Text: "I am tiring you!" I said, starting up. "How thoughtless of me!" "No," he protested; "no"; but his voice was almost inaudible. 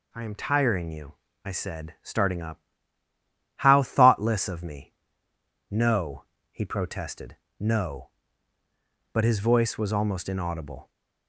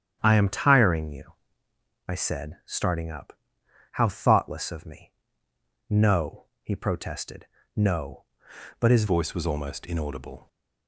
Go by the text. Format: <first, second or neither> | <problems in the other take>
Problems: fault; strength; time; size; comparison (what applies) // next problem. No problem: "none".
first | starts louder than the rest; strong; until 1.2 s; 9 dB // changes voice at "voice"; from 9.0 s on; 1.4 s long